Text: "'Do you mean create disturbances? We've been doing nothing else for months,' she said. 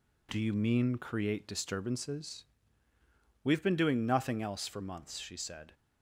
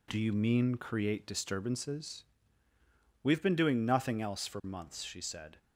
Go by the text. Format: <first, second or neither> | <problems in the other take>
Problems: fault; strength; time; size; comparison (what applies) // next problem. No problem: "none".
neither | none